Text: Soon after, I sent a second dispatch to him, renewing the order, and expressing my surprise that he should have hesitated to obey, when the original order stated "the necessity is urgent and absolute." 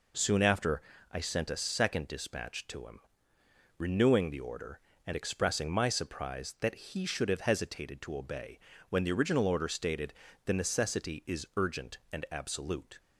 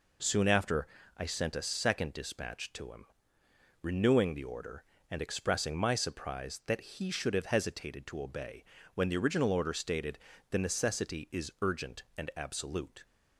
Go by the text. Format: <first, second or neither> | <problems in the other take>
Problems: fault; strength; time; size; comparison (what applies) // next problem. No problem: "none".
neither | pauses between "stated" and "the"; slight; the same in both